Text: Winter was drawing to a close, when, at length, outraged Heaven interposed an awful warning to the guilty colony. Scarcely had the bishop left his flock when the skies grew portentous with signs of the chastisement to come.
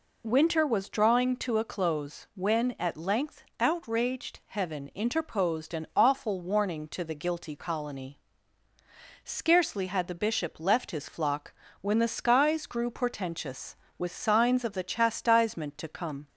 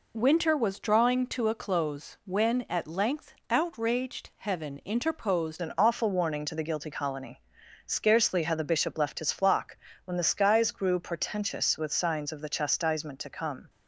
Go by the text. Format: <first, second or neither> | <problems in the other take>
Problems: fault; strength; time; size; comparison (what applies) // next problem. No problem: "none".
first | changes voice at "an"; from 5.6 s on; 8.0 s long // pauses between "flock" and "when"; slight; at 9.7 s; 0.28 s long; slight in the first